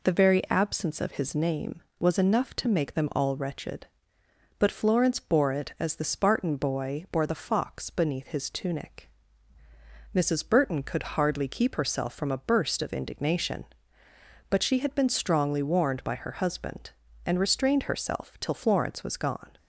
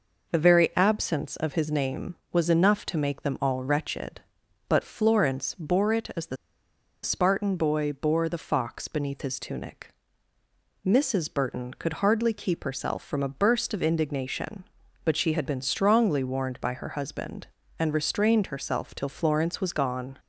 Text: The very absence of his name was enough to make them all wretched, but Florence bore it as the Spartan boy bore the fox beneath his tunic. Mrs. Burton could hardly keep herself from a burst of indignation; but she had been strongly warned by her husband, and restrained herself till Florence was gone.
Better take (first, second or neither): first